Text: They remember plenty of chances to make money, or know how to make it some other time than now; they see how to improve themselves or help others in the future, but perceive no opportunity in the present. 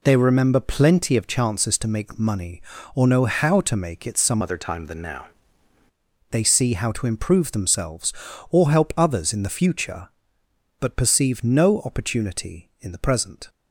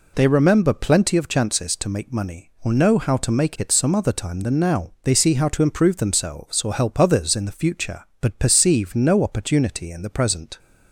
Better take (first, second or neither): second